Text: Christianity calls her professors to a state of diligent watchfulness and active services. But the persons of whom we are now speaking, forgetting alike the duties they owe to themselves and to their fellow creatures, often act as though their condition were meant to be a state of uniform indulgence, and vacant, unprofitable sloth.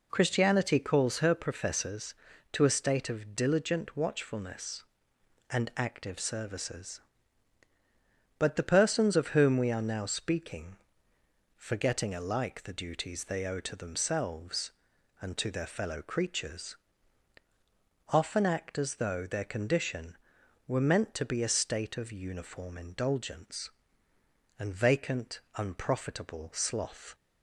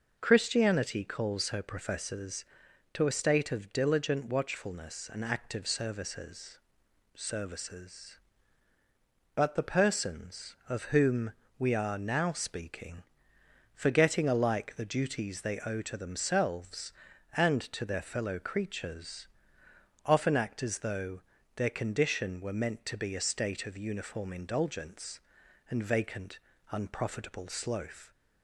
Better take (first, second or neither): first